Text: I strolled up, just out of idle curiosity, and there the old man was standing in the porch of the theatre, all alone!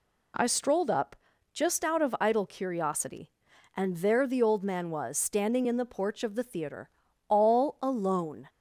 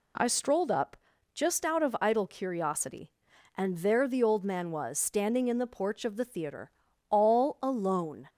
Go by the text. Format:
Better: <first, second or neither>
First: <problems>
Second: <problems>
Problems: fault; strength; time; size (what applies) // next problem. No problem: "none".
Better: neither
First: none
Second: none